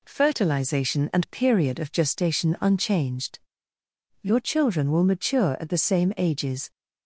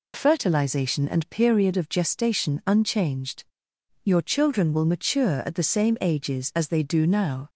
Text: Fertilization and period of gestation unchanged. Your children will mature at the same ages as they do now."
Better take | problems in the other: second | stops before "as they do now"; at 6.7 s

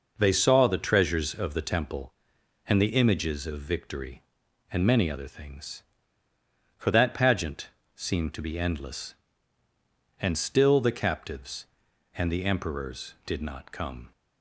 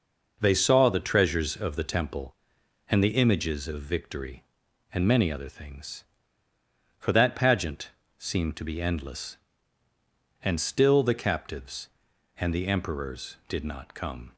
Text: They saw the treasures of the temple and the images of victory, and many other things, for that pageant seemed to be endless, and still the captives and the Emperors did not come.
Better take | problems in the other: neither | pauses between "pageant" and "seemed"; slight; the same in both

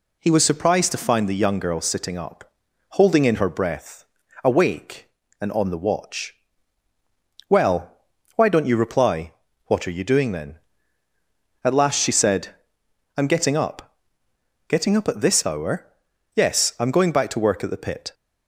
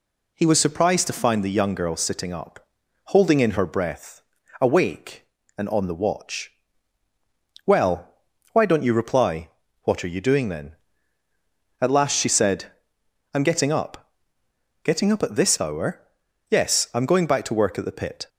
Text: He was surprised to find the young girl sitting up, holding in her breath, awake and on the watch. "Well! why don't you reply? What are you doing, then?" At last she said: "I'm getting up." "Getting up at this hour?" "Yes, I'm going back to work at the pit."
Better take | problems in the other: neither | none

